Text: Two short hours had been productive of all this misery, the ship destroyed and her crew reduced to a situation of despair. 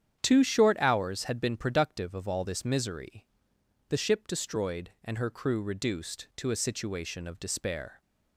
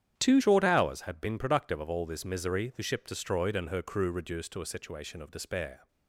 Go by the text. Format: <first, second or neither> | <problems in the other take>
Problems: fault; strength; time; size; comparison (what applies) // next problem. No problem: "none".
first | starts louder than the rest; strong; until 1.1 s; 9.5 dB; strong in the first // changes voice at "short"; from 0.4 s on; 5.4 s long